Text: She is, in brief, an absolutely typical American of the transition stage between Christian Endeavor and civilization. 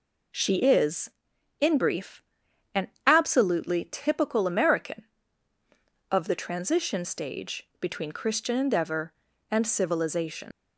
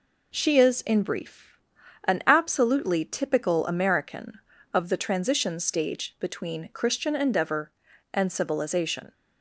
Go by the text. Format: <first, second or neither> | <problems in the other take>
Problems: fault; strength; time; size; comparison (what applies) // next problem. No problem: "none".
second | pauses between "an" and "absolutely"; slight; at 2.8 s; 0.18 s long // leaves "civilization" unfinished; at 10.5 s; 105 ms